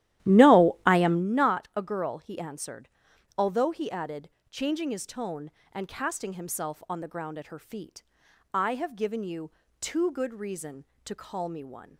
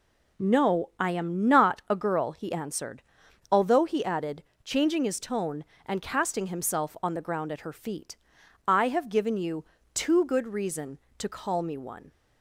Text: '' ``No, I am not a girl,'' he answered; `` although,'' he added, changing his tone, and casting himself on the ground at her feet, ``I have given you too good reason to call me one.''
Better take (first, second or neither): second